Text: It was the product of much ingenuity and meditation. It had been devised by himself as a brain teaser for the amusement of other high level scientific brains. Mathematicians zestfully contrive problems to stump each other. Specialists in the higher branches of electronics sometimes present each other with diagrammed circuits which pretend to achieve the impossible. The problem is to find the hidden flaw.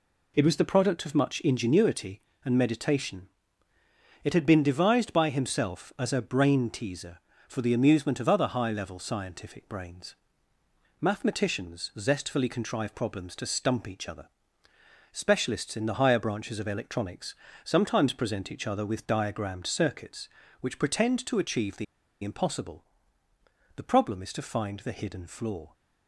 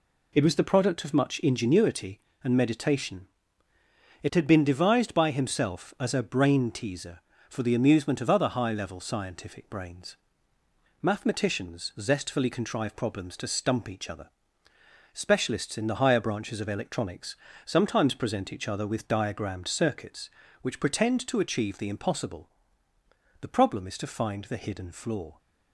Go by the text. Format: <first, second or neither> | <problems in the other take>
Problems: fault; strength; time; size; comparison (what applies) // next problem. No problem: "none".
second | pauses between "electronics" and "sometimes"; slight; at 17.3 s; 0.28 s long; slight in the second // pauses between "the" and "impossible"; at 21.8 s; 0.38 s long